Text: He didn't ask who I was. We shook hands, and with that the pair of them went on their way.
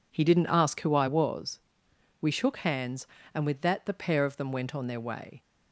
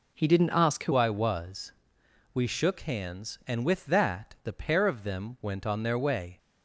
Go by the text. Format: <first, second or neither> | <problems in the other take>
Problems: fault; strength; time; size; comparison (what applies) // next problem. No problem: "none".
first | changes voice at "I"; from 0.9 s on; 5.4 s long